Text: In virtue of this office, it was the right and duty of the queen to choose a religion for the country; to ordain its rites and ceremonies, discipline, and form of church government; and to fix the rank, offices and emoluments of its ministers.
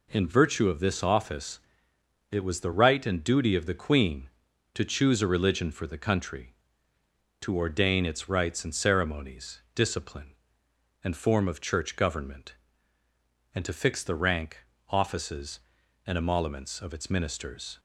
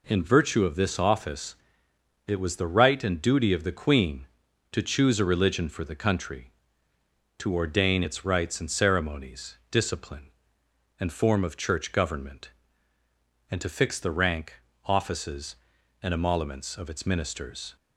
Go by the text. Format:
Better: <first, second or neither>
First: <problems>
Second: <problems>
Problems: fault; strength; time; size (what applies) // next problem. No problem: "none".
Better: neither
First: none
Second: none